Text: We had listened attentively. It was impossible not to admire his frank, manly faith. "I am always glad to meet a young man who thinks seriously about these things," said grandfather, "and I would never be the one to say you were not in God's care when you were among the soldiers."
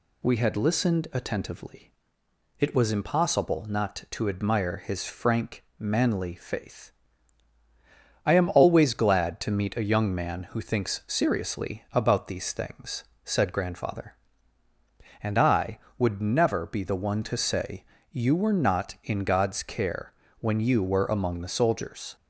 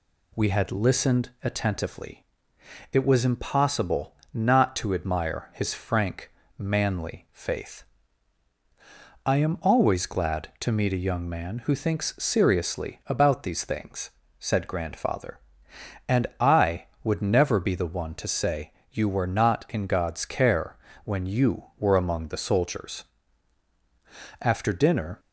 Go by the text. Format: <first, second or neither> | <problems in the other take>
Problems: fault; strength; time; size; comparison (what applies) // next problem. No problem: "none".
first | pauses between "impossible" and "not"; slight; at 4.1 s; 0.18 s long // pauses between "say" and "you"; slight; at 18.7 s; 0.20 s long; slight in the first // pauses between "care" and "when"; slight; at 20.7 s; 0.26 s long; slight in the first // goes on to say "After dinner"; noticeable; from 24.4 s on; 0.78 s long